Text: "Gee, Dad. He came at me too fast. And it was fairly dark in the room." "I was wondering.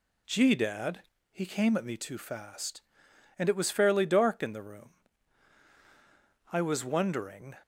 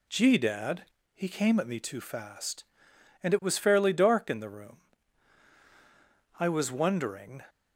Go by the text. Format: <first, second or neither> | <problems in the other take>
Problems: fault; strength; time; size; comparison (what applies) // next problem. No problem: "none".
neither | none